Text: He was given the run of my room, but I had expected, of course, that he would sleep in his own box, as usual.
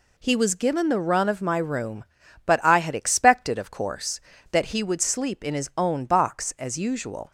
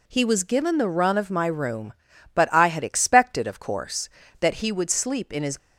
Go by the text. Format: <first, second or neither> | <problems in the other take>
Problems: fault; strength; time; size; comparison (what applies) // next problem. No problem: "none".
first | stops before "own box as usual"; at 5.5 s